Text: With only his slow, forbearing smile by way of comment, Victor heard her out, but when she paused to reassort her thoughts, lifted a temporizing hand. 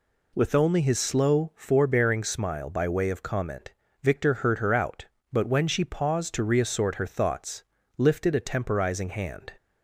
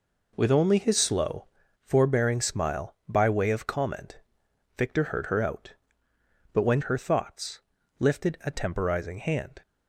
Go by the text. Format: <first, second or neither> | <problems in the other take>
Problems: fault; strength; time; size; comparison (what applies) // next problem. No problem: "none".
first | skips "she paused to reassort"; at 6.8 s